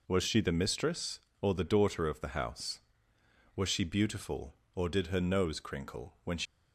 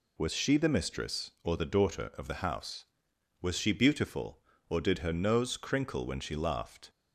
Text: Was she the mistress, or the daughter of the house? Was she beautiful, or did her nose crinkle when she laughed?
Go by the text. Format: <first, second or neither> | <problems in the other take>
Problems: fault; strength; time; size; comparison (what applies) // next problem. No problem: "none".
second | stops before "laughed"; at 6.4 s